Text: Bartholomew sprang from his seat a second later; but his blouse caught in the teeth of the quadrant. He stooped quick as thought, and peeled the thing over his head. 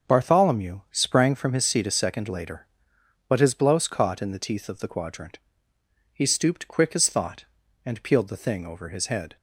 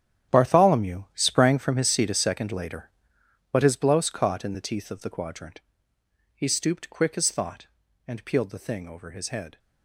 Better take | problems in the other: first | gets quieter; strong; throughout; 15 dB // starts louder than the rest; strong; until 1.4 s; 10.5 dB; also in the first

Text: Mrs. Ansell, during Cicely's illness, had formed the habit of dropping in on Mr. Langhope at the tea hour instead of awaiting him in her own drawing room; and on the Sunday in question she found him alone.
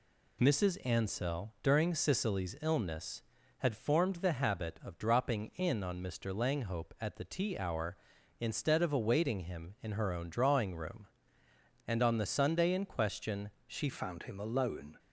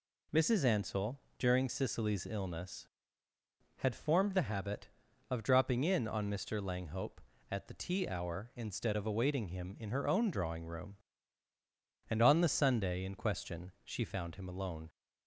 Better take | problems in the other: second | pauses between "question" and "she"; slight; at 13.4 s; 0.18 s long // changes voice at "found"; from 13.9 s on; 1.0 s long

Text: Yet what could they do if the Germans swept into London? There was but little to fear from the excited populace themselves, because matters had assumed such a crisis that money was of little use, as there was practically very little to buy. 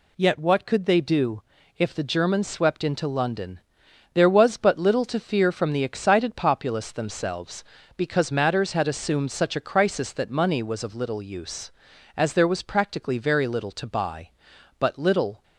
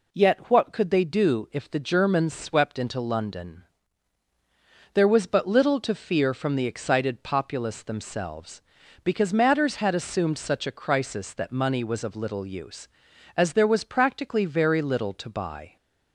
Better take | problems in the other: second | pauses between "do" and "if"; slight; at 1.4 s; 0.34 s long // goes on to say "But little"; noticeable; from 14.7 s on; 0.64 s long

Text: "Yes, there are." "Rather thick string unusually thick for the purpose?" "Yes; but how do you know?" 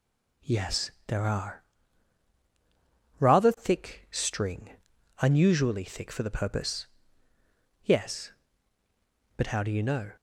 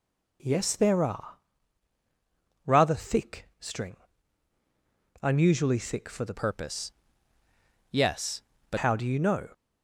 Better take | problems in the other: first | pauses between "string" and "unusually"; strong; at 3.9 s; 1.2 s long; noticeable in the first // changes voice from "purpose" to "but"; from 6.3 to 8.7 s; 2.4 s long

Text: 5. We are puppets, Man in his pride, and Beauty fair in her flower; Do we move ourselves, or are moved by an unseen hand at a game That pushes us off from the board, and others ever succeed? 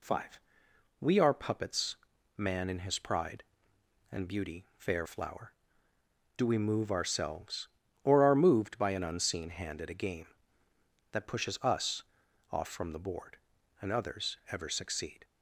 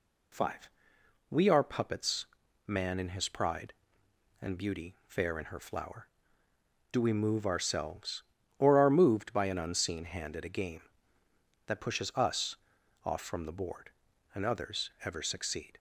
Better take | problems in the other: second | skips "in her"; at 5.0 s // pauses between "us" and "off"; noticeable; at 12.0 s; 0.48 s long; noticeable in the second

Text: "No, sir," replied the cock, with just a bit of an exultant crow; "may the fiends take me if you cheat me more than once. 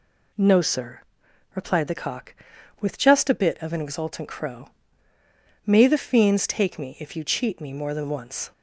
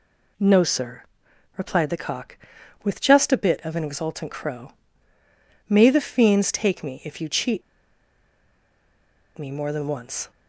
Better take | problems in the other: first | pauses between "cheat" and "me"; strong; at 7.6 s; 1.7 s long

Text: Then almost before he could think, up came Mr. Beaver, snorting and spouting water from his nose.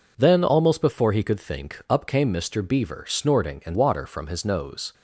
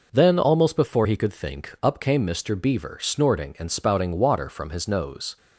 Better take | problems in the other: second | skips "spouting"; at 3.7 s

